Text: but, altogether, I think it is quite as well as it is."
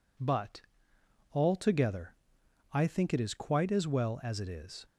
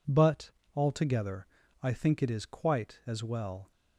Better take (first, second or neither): first